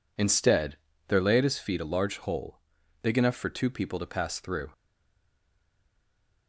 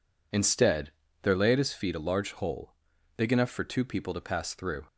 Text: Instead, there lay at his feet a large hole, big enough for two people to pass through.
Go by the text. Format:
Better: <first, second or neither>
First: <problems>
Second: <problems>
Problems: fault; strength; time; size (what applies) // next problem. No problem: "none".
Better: second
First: stays silent after the last word; noticeable; from 4.7 s on; 1.7 s long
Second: none